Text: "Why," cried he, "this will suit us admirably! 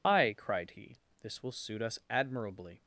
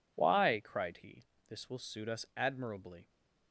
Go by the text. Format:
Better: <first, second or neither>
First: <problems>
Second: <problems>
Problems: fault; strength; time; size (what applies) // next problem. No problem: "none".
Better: second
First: loses the start of "Why"; at 0.0 s; 165 ms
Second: none